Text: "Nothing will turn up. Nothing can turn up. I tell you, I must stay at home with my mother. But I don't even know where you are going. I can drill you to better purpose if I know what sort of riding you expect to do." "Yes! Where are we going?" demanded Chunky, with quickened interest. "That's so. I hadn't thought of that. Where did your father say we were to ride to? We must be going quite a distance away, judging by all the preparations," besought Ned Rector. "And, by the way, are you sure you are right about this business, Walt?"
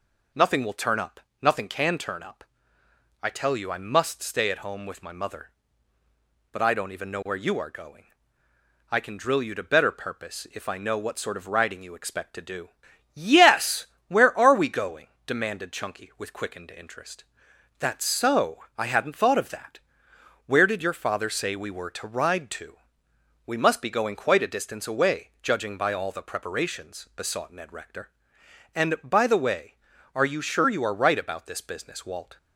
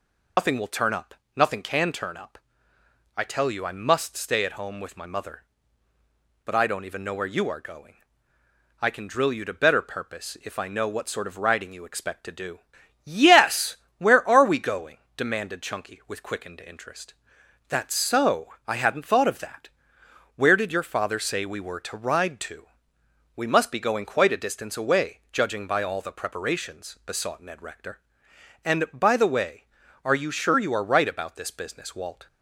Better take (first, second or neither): first